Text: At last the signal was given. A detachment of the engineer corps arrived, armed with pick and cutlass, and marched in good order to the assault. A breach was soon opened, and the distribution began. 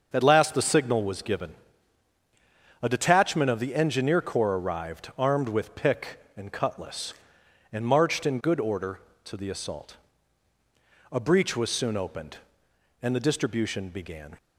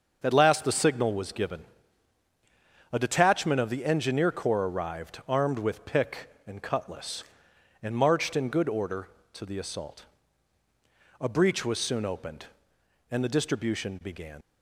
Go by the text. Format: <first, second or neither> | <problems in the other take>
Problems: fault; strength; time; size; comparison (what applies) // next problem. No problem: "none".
first | starts louder than the rest; until 1.2 s; 6.5 dB; also in the first // leaves "began" unfinished; at 14.4 s; 60 ms